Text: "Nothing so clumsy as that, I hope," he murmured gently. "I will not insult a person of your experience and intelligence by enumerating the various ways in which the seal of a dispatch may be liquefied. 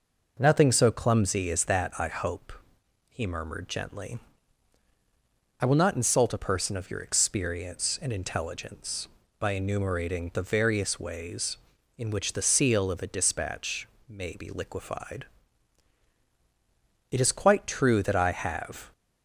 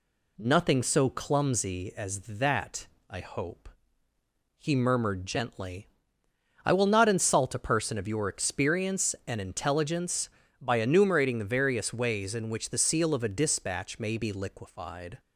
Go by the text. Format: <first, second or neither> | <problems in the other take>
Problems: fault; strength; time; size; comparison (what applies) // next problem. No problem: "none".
second | pauses between "dispatch" and "may"; slight; at 13.8 s; 0.20 s long // goes on to say "It is quite true that I have"; strong; from 17.0 s on; 1.8 s long